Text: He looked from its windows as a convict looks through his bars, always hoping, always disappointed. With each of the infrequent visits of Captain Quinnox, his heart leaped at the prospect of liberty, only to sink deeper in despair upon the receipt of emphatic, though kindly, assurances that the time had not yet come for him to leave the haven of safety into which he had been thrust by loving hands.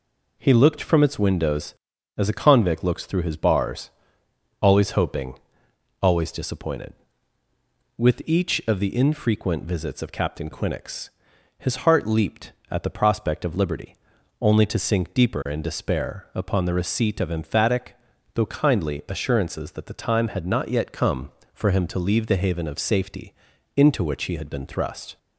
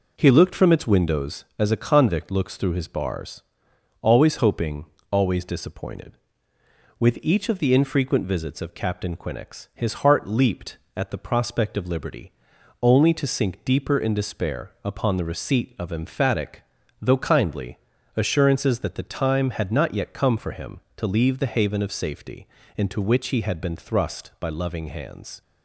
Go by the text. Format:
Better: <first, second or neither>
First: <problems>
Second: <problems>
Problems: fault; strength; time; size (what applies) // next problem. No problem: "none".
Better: second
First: pauses between "safety" and "into"; at 23.3 s; 0.44 s long // stops before "by loving hands"; at 25.1 s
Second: pauses between "safety" and "into"; slight; at 22.4 s; 0.30 s long